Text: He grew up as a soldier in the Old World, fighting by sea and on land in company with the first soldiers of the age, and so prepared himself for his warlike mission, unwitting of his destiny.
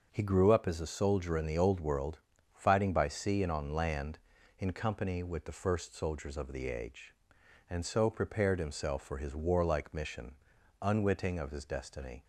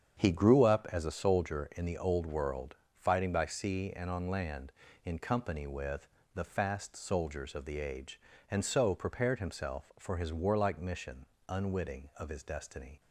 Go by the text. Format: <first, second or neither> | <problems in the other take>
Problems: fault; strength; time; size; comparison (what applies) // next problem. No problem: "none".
first | starts louder than the rest; strong; until 1.2 s; 7.5 dB; also in the first // pauses between "with" and "the"; slight; at 6.0 s; 0.26 s long // says "fast" for "first"; at 6.4 s